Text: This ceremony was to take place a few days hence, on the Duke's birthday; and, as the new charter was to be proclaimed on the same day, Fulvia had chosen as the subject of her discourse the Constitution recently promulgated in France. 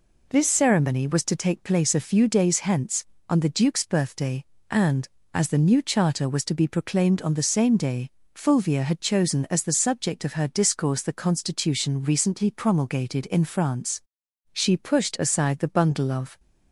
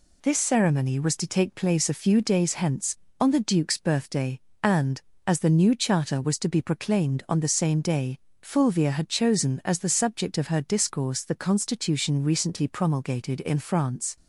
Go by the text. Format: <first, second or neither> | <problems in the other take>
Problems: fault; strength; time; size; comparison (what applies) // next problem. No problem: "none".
second | goes on to say "She pushed aside the bundle of"; strong; from 14.5 s on; 1.8 s long